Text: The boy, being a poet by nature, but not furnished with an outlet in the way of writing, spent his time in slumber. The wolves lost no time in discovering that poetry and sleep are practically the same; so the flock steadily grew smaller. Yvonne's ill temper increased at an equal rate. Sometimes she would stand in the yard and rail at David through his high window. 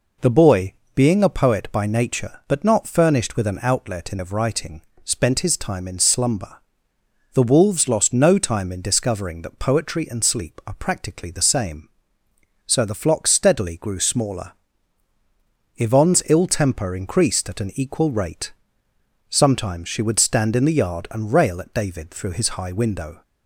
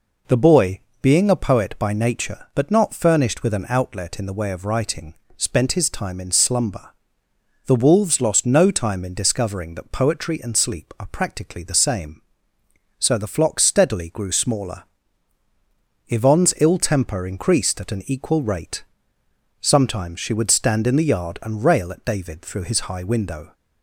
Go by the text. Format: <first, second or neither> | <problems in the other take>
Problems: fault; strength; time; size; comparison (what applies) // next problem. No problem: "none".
second | skips "the way"; at 4.1 s